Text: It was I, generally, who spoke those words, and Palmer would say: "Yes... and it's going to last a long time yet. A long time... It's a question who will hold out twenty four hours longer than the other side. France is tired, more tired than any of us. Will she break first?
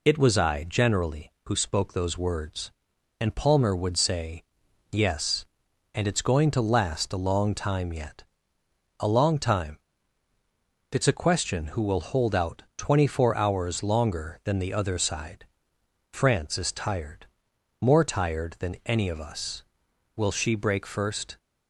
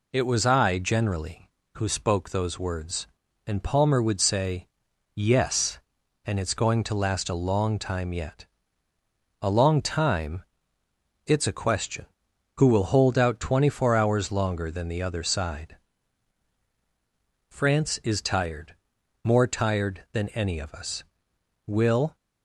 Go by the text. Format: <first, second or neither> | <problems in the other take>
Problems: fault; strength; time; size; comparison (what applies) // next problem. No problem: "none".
first | stops before "she break first"; at 22.1 s